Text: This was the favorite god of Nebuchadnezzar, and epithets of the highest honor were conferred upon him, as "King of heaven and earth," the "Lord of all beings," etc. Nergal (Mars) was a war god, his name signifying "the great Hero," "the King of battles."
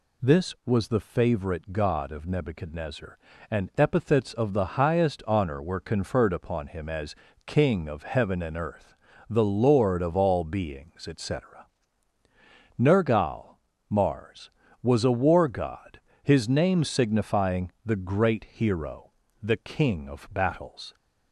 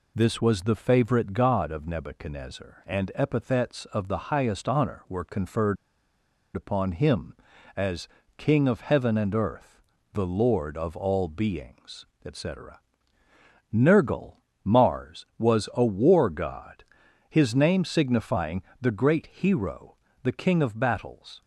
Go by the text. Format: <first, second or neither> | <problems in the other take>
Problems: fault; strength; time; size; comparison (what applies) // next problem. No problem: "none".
first | pauses between "conferred" and "upon"; noticeable; at 5.7 s; 0.79 s long // pauses between "as" and "King"; slight; at 8.0 s; 0.30 s long; slight in the first // pauses between "signifying" and "the"; slight; at 18.6 s; 0.18 s long